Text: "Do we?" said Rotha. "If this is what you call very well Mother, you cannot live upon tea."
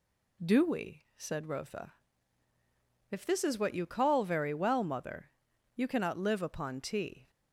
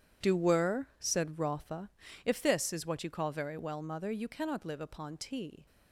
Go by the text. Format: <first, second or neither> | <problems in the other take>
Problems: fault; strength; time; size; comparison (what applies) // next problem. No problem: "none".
first | says "were" for "we"; at 0.3 s